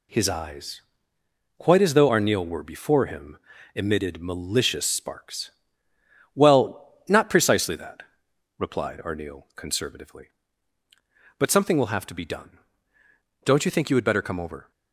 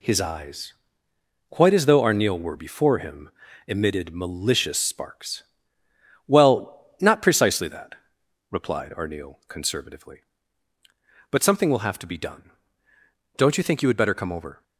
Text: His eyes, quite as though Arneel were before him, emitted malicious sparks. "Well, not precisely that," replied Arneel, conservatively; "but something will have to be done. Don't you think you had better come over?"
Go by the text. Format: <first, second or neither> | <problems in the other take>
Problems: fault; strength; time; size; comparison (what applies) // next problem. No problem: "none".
neither | none